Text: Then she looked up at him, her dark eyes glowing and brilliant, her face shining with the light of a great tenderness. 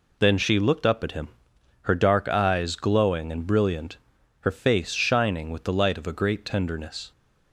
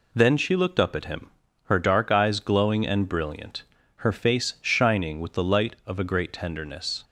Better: neither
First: none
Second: none

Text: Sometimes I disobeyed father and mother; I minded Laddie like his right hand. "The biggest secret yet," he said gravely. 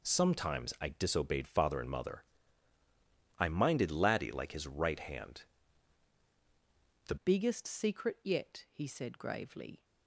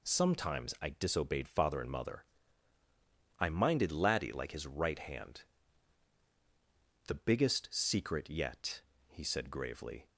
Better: second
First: changes voice at "biggest"; from 7.1 s on; 2.7 s long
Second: none

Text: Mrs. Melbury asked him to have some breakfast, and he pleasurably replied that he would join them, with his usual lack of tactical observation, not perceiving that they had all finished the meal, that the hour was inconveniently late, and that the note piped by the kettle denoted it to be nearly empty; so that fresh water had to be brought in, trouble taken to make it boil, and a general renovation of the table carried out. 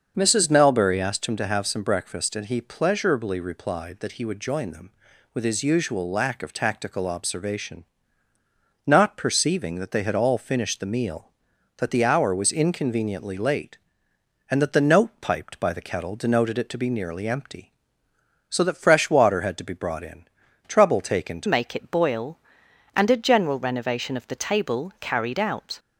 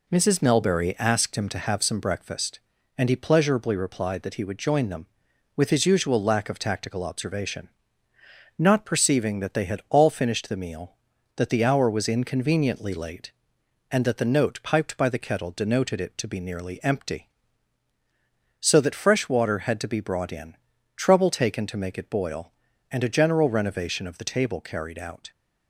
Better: second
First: starts louder than the rest; until 1.1 s; 6.5 dB // changes voice at "make"; from 21.4 s on; 4.3 s long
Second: none

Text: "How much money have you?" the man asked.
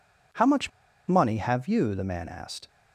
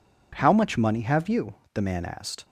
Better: second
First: pauses between "much" and "money"; at 0.6 s; 0.38 s long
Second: none

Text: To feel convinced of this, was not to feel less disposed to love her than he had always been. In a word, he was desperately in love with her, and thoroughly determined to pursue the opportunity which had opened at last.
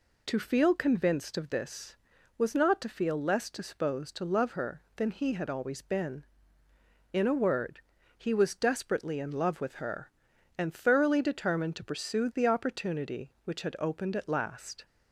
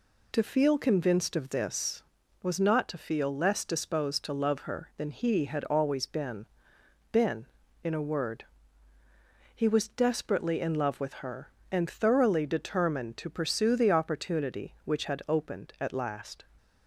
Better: first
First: none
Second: says "been" twice; at 7.1 s

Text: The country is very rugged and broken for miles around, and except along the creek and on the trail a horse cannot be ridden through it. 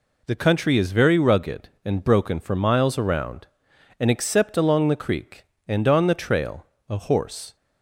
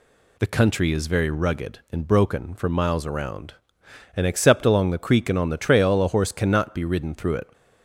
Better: second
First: pauses between "trail" and "a"; slight; at 6.6 s; 0.22 s long // stops before "cannot be ridden through it"; at 7.5 s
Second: none

